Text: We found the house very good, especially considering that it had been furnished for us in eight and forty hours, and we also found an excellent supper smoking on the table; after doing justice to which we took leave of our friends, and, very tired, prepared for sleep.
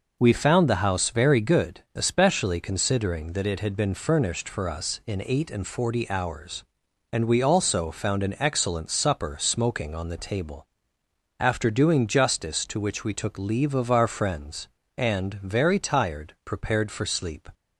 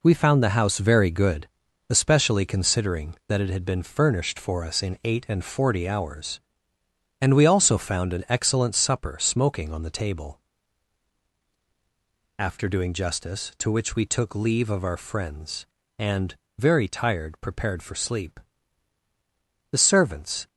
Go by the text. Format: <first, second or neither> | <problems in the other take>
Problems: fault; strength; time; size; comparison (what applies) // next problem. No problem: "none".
first | goes on to say "The servants"; noticeable; from 19.7 s on; 0.76 s long